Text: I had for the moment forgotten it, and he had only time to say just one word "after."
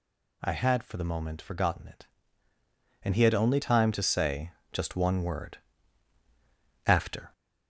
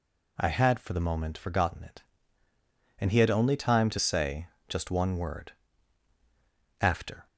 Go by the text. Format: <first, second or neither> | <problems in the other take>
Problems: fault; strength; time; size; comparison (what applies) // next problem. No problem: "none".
second | gets louder; slight; throughout; 3 dB // pauses between "say" and "just"; slight; at 4.5 s; 0.20 s long; slight in the second // pauses between "word" and "after"; strong; at 5.5 s; 1.2 s long; strong in the second